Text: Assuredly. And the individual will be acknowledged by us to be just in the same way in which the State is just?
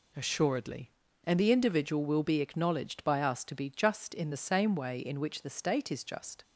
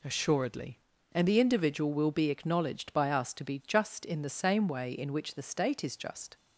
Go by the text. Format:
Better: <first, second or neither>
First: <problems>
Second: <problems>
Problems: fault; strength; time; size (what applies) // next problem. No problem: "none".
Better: neither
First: none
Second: none